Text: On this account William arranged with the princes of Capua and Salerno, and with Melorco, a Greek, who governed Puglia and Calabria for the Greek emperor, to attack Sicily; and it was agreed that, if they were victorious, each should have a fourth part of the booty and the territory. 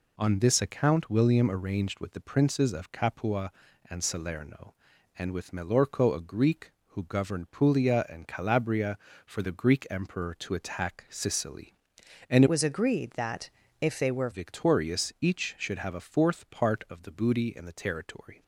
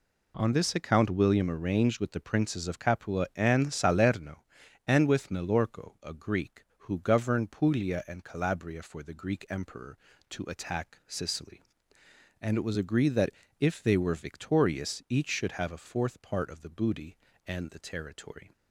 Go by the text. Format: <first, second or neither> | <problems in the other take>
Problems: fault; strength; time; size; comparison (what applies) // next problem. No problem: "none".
second | changes voice from "was" to "were"; from 12.4 to 14.2 s; 1.8 s long